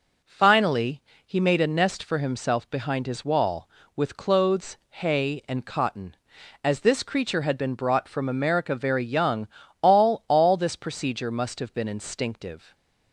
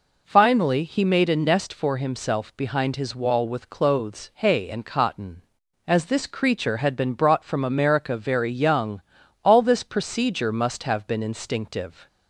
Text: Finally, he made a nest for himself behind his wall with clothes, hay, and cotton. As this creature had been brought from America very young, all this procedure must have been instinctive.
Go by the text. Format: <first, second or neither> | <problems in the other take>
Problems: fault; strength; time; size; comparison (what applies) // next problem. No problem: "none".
second | says "all" twice; at 10.2 s